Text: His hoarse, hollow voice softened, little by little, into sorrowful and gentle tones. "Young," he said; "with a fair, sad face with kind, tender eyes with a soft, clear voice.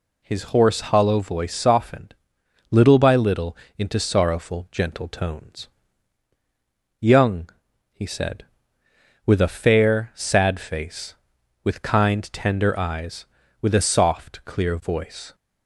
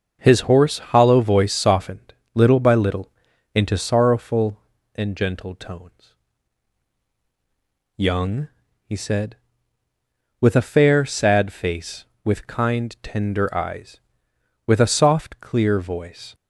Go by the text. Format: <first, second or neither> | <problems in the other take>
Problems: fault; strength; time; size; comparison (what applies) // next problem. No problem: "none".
second | skips "and"; at 4.7 s